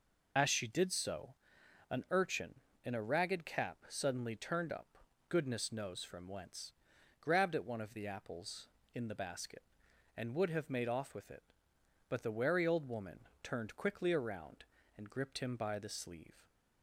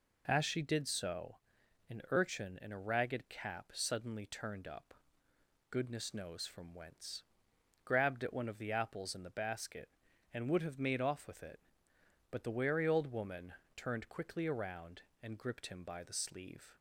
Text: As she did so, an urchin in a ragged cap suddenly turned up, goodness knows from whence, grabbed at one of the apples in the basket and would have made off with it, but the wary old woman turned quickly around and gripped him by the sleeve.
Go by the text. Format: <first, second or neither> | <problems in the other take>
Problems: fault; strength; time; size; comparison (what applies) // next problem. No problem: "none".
second | loses the start of "As"; at 0.3 s; 35 ms // pauses between "woman" and "turned"; slight; at 13.2 s; 0.20 s long; slight in the second